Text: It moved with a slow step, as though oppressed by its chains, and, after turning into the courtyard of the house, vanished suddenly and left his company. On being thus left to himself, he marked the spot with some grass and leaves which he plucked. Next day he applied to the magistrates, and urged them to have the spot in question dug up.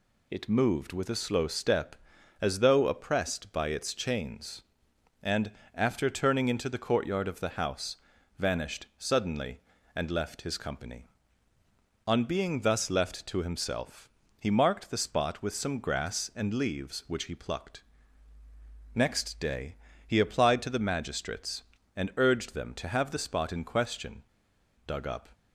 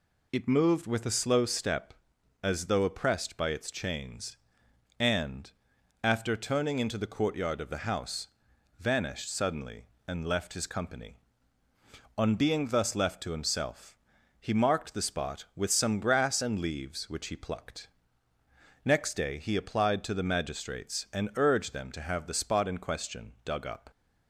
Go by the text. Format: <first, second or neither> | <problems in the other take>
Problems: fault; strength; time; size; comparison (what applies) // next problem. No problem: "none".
second | pauses between "day" and "he"; slight; at 19.7 s; 0.30 s long // pauses between "question" and "dug"; noticeable; at 24.2 s; 0.62 s long